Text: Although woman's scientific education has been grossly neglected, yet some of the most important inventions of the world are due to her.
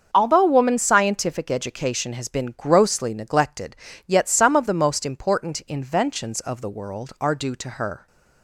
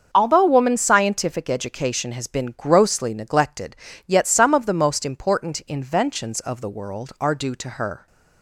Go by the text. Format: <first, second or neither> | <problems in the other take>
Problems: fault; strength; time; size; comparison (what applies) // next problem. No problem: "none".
neither | starts louder than the rest; the same in both